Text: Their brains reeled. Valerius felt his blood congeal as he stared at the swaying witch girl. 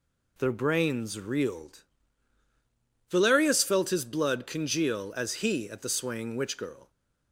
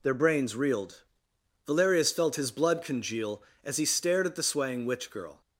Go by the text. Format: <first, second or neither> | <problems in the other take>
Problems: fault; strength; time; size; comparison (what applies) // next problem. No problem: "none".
second | skips "stared"; at 5.7 s